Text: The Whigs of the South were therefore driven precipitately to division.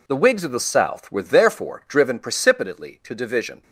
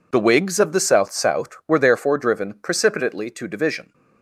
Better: first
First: none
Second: says "South" twice; at 1.1 s

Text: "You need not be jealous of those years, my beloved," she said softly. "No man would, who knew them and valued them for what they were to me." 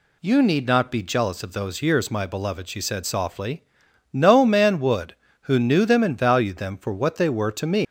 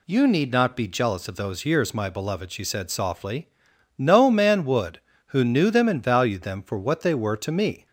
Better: second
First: leaves "me" unfinished; at 7.8 s; 155 ms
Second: none

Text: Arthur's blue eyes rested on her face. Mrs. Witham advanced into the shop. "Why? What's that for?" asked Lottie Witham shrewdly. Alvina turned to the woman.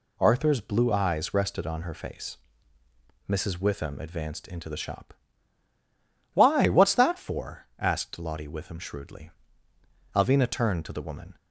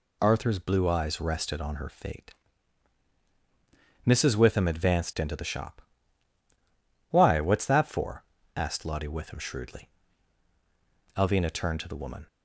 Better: first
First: none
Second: says "fate" for "face"; at 1.8 s

